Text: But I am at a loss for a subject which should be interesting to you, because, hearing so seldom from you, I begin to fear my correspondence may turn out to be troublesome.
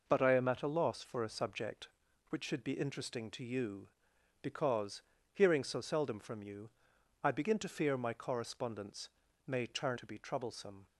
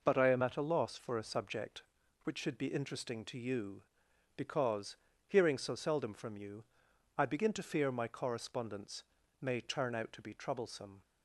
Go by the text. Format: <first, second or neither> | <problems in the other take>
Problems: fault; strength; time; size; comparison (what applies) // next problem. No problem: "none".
second | pauses between "correspondence" and "may"; at 9.0 s; 0.38 s long; also in the second // skips "out"; at 9.9 s